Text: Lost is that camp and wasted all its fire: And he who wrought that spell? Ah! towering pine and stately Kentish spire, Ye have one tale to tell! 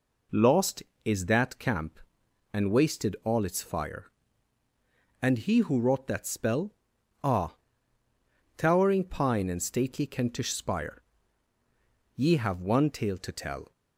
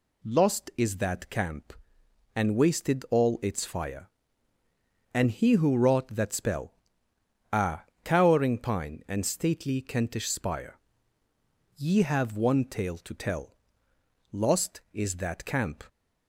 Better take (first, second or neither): first